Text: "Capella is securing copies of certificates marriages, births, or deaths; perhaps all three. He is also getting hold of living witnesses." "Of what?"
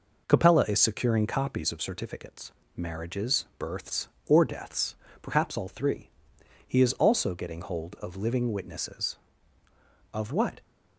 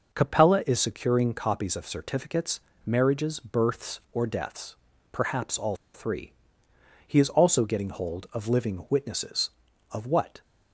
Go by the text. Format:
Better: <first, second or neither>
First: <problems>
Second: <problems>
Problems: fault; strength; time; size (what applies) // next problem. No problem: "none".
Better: first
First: pauses between "certificates" and "marriages"; slight; at 2.5 s; 0.24 s long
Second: pauses between "certificates" and "marriages"; slight; at 2.5 s; 0.24 s long // pauses between "all" and "three"; slight; at 5.7 s; 0.20 s long